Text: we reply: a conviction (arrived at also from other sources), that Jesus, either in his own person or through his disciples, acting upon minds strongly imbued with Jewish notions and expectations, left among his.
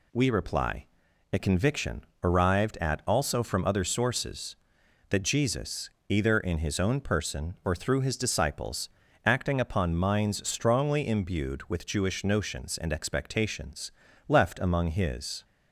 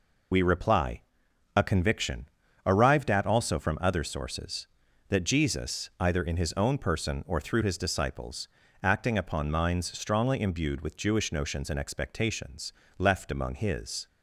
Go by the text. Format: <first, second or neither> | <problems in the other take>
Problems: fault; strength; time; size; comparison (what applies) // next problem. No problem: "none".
first | loses the start of "we"; at 0.3 s; 65 ms